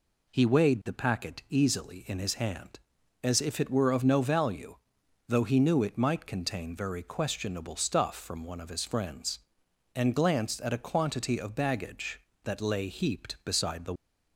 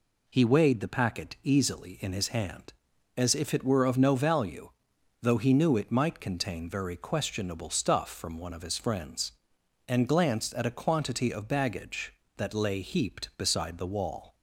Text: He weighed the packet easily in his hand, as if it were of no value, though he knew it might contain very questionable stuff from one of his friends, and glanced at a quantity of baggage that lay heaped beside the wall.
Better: second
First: stops before "wall"; at 13.9 s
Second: none

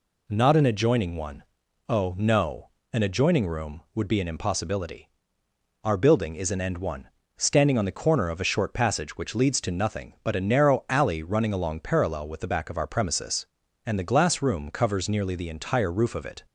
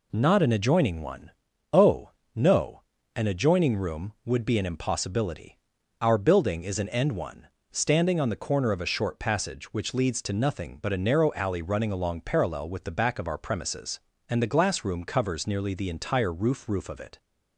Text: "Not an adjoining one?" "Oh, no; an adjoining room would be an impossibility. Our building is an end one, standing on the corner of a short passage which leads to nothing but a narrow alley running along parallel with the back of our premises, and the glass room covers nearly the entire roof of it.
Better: first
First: none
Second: says "roof" twice; at 16.6 s

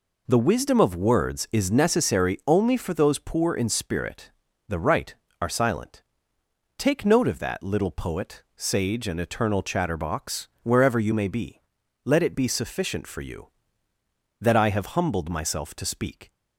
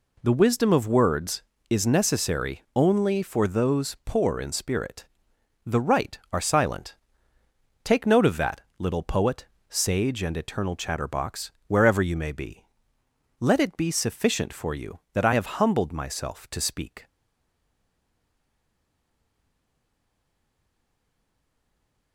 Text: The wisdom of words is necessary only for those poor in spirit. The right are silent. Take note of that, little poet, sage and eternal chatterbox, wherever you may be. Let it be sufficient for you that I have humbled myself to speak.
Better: first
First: none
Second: stays silent after the last word; strong; from 17.0 s on; 5.1 s long

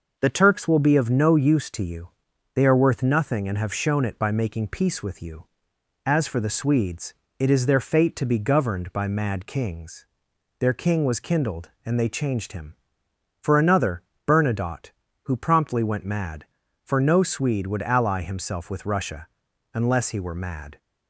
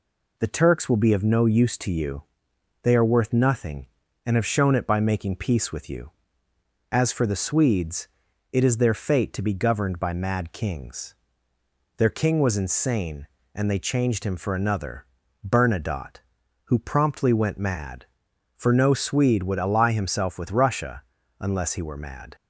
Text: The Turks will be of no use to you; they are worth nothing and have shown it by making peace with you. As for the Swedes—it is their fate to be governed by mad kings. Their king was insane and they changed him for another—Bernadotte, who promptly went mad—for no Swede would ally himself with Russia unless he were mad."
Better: second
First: says "kindled" for "insane"; at 11.1 s // pauses between "Russia" and "unless"; at 19.2 s; 0.44 s long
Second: pauses between "Russia" and "unless"; slight; at 21.0 s; 0.36 s long

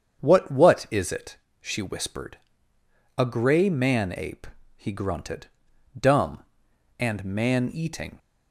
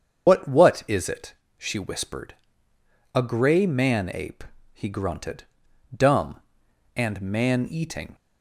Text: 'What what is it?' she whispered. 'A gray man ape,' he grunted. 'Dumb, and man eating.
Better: first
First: starts louder than the rest; strong; until 1.2 s; 7.5 dB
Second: loses the start of "What"; at 0.2 s; 100 ms // starts louder than the rest; strong; until 1.3 s; 7 dB

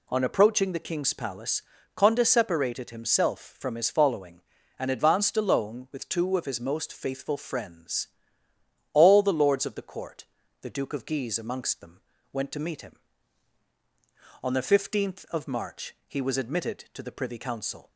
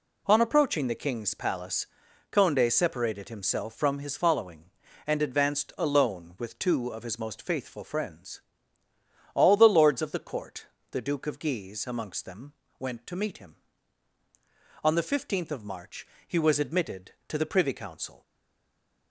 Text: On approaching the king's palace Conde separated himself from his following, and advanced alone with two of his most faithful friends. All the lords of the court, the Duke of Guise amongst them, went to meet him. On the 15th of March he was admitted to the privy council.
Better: first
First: pauses between "palace" and "Conde"; slight; at 1.6 s; 0.32 s long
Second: pauses between "palace" and "Conde"; noticeable; at 1.8 s; 0.46 s long // pauses between "March" and "he"; slight; at 16.0 s; 0.18 s long // stays silent after the last word; slight; from 18.2 s on; 0.9 s long

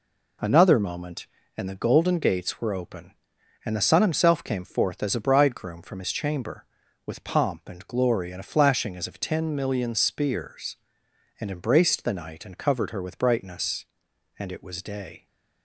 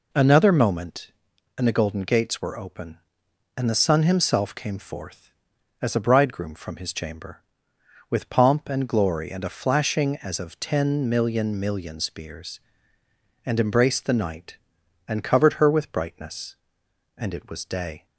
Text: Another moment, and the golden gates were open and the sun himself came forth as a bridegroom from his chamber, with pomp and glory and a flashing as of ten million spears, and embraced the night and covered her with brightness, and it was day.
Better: first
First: none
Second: says "million" twice; at 11.5 s

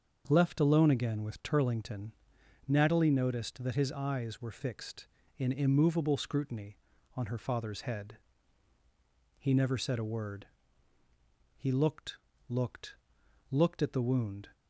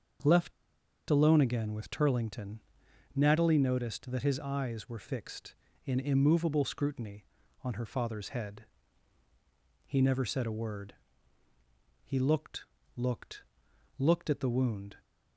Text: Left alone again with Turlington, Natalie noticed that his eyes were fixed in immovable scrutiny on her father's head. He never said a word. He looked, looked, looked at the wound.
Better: first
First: starts louder than the rest; until 1.2 s; 6.5 dB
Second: starts louder than the rest; until 1.8 s; 6.5 dB // pauses between "Left" and "alone"; noticeable; at 0.5 s; 0.57 s long

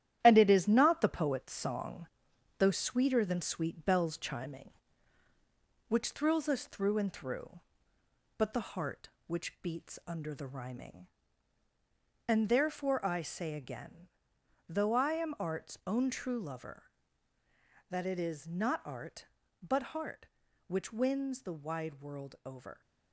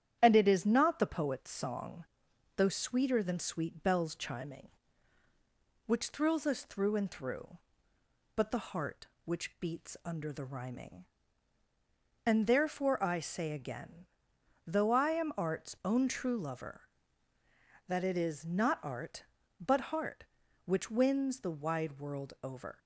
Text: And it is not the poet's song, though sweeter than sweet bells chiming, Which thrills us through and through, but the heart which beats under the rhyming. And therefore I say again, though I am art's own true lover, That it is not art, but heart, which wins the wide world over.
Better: second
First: gets quieter; throughout; 6 dB // starts louder than the rest; strong; until 1.2 s; 11.5 dB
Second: starts louder than the rest; strong; until 1.2 s; 10.5 dB

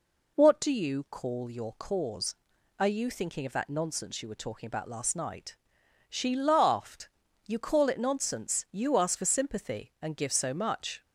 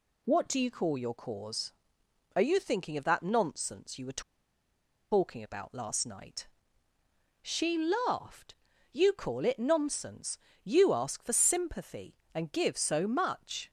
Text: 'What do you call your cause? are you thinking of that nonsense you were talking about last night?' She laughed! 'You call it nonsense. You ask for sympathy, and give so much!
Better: first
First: none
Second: pauses between "were" and "talking"; noticeable; at 4.2 s; 0.91 s long

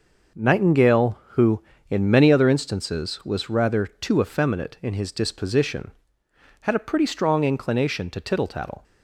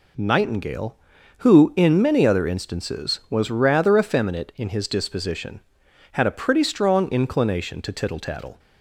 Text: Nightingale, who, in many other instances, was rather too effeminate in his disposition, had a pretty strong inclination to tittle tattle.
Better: first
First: none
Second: skips "too"; at 3.9 s

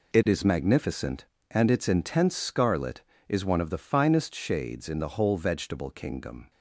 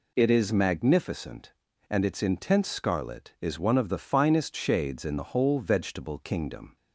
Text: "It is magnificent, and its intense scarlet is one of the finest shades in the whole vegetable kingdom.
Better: second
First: gets quieter; strong; throughout; 10.5 dB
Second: none

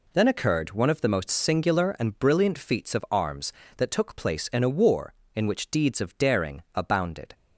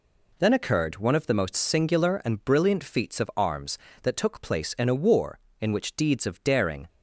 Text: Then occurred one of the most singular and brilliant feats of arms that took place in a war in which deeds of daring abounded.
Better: first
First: none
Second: stops before "abounded"; at 6.8 s

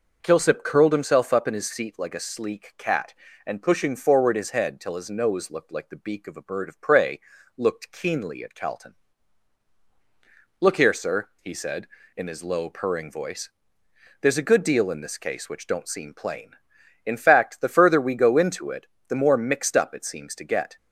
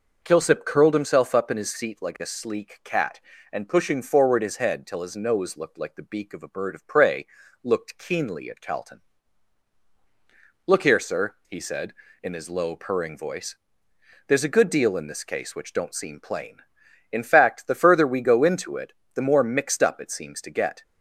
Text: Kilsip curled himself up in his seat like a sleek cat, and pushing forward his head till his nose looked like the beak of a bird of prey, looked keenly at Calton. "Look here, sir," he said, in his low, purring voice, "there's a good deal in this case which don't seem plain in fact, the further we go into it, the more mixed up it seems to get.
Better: neither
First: none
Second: none

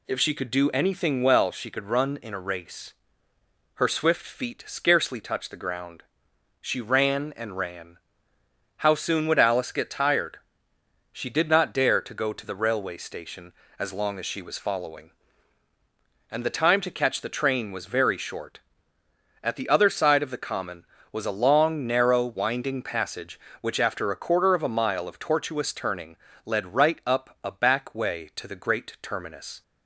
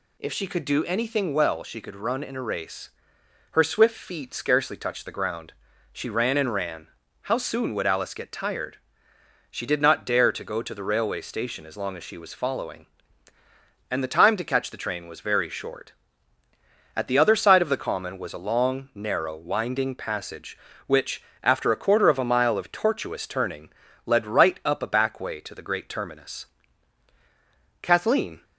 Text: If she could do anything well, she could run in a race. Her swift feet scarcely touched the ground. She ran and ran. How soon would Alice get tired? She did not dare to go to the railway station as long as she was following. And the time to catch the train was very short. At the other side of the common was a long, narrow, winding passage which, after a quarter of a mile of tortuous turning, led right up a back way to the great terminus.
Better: first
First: none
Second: goes on to say "Kathleen"; noticeable; from 27.8 s on; 0.62 s long

